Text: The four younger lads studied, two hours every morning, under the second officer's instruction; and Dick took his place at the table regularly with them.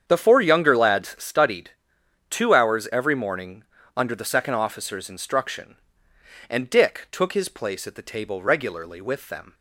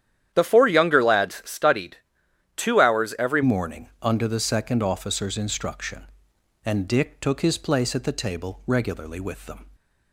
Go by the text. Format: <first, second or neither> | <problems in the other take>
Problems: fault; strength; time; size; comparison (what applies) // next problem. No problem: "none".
first | starts louder than the rest; strong; until 1.3 s; 10.5 dB; strong in the first // changes voice at "morning"; from 3.4 s on; 6.2 s long